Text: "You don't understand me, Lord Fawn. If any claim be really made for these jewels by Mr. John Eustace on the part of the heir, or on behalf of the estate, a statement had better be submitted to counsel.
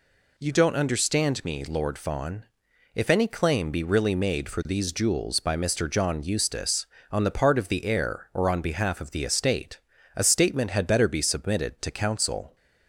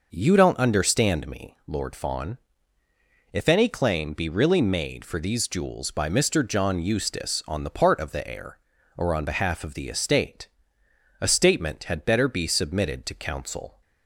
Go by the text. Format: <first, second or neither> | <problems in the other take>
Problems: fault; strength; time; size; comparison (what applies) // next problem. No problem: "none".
neither | none